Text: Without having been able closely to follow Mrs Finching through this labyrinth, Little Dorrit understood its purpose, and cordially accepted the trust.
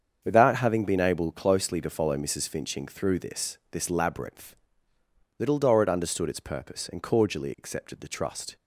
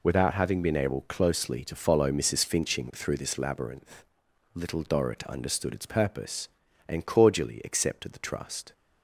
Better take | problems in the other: second | starts louder than the rest; strong; until 1.2 s; 7 dB // says "this" twice; at 3.7 s

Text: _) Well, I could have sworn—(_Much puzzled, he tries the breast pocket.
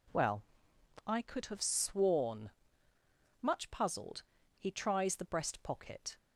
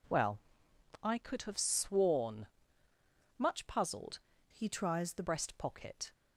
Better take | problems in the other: first | changes voice from "he" to "the"; from 4.5 to 5.2 s; 0.7 s long

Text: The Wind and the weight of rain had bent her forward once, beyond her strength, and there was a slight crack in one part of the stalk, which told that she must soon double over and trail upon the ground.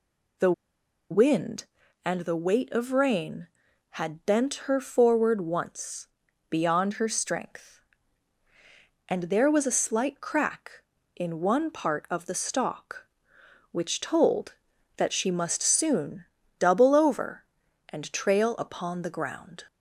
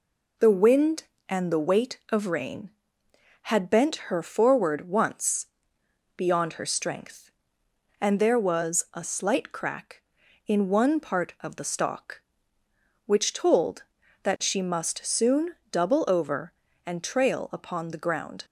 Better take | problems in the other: second | pauses between "The" and "Wind"; noticeable; at 0.5 s; 0.59 s long // pauses between "soon" and "double"; slight; at 16.2 s; 0.34 s long; slight in the second

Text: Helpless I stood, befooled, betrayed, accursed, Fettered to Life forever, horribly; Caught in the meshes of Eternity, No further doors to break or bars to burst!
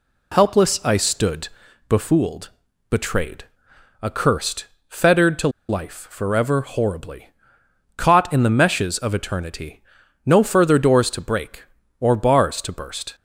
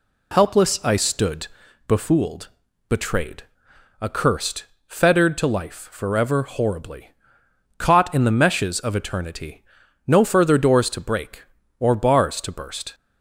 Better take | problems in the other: second | pauses between "to" and "Life"; slight; at 5.4 s; 0.20 s long

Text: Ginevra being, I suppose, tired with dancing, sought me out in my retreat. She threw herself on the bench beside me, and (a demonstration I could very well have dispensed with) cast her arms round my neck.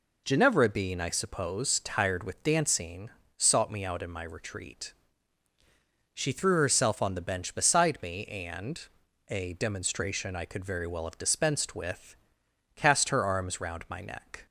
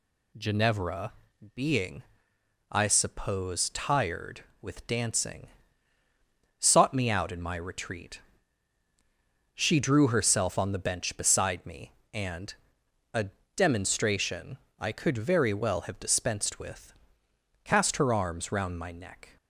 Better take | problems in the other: first | pauses between "Ginevra" and "being"; at 1.1 s; 0.42 s long // says "drew" for "threw"; at 9.7 s // pauses between "a" and "demonstration"; slight; at 13.2 s; 0.30 s long // pauses between "demonstration" and "I"; slight; at 14.5 s; 0.22 s long

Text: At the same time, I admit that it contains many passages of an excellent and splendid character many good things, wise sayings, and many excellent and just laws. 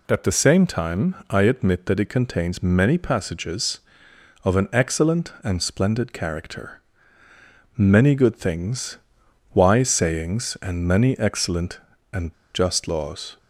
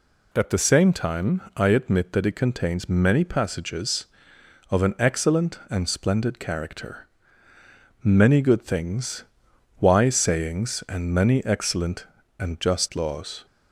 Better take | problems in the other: second | pauses between "character" and "many"; noticeable; at 6.8 s; 0.96 s long; noticeable in the second // pauses between "and" and "just"; slight; at 12.3 s; 0.20 s long

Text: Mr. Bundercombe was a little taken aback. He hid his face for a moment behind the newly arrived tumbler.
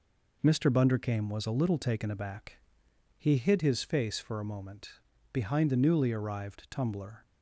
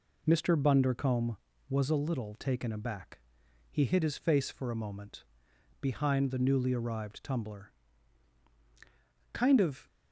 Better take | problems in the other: first | pauses between "moment" and "behind"; noticeable; at 5.2 s; 0.58 s long; also in the first // goes on to say "Kind of"; from 9.3 s on; 0.54 s long

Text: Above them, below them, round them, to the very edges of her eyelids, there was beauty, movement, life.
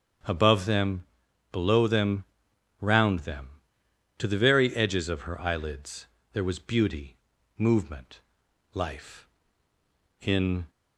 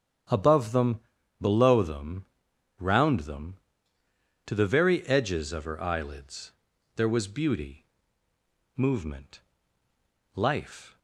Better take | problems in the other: second | starts louder than the rest; strong; until 1.7 s; 8 dB; strong in the second // goes on to say "In"; slight; from 10.2 s on; 0.48 s long

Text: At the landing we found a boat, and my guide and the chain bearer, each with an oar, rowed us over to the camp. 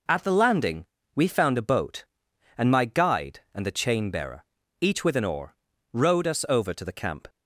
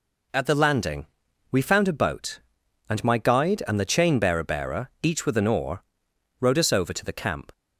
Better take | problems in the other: first | pauses between "landing" and "we"; at 1.0 s; 0.44 s long; slight in the first // says "bearer" twice; at 4.4 s

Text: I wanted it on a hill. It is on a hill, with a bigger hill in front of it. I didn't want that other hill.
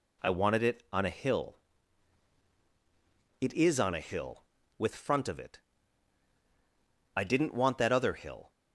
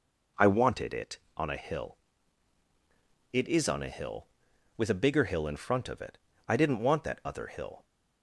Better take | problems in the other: second | skips "a bigger hill in"; at 4.9 s

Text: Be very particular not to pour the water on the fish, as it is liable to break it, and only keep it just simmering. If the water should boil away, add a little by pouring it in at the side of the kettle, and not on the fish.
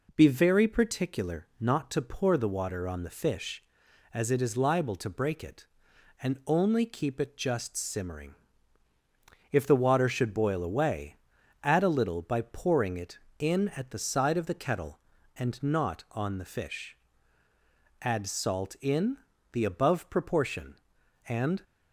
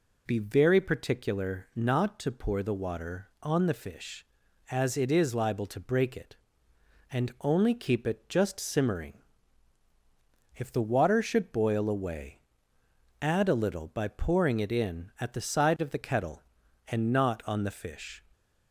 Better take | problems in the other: second | goes on to say "Add salt in the above proportion and"; strong; from 18.0 s on; 3.6 s long

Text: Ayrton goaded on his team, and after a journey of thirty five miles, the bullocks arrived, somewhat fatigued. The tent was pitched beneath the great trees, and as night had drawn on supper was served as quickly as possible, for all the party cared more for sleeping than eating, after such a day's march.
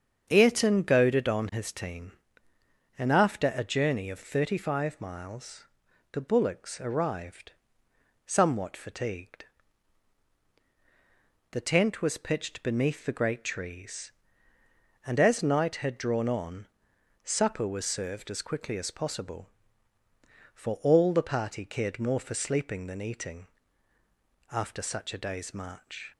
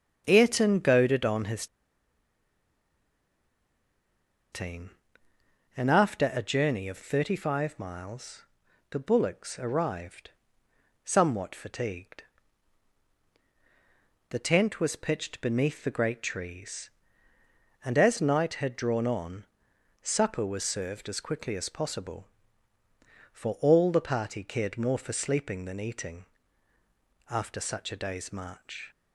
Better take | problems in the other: first | starts louder than the rest; strong; until 1.2 s; 7.5 dB; strong in the first // pauses between "his" and "team"; strong; at 1.6 s; 2.8 s long // pauses between "on" and "supper"; noticeable; at 19.4 s; 0.58 s long; noticeable in the first

